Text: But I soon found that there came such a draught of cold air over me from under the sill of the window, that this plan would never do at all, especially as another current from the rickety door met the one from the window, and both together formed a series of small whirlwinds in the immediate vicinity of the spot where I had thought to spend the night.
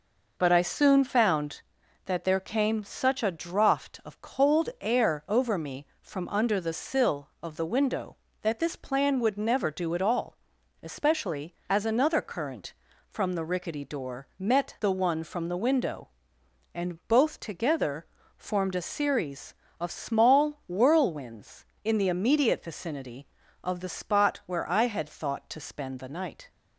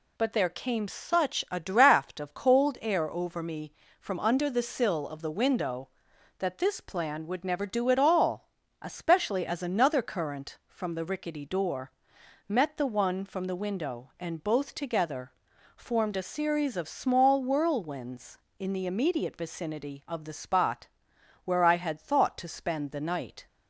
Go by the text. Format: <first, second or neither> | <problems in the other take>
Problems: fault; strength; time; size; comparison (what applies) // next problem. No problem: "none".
first | skips "I soon found that"; at 0.3 s // pauses between "door" and "met"; noticeable; at 11.8 s; 0.58 s long // pauses between "together" and "formed"; at 15.3 s; 0.44 s long; slight in the first // pauses between "spot" and "where"; noticeable; at 20.8 s; 0.56 s long